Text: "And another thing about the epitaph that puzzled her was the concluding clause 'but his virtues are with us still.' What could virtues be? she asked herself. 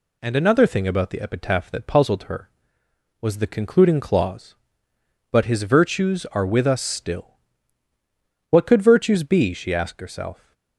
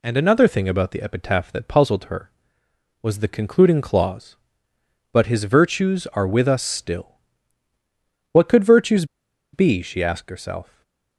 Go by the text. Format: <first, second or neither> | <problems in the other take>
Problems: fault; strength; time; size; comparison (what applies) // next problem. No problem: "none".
first | pauses between "virtues" and "be"; noticeable; at 9.0 s; 0.48 s long // stays silent after the last word; slight; from 10.6 s on; 0.5 s long